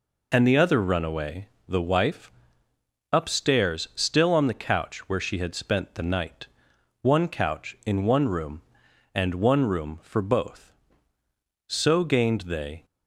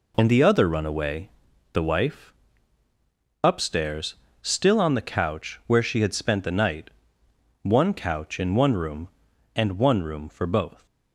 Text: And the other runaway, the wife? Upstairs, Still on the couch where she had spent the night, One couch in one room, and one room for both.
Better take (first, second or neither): second